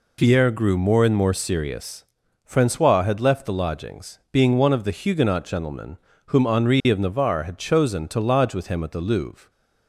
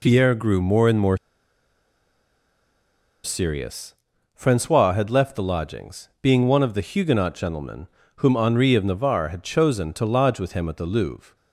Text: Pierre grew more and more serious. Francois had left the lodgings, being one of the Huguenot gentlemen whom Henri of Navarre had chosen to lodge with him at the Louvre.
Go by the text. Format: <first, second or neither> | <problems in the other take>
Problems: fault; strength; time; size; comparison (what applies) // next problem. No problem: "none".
first | pauses between "more" and "serious"; strong; at 1.1 s; 2.0 s long // pauses between "gentlemen" and "whom"; slight; at 7.8 s; 0.28 s long; slight in the first